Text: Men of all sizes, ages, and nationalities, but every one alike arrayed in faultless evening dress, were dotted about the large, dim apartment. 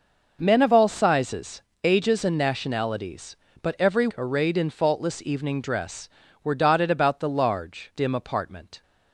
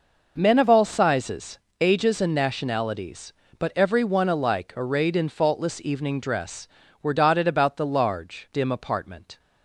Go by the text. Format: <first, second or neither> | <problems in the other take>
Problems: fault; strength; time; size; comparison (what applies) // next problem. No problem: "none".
second | skips "one alike"; at 4.1 s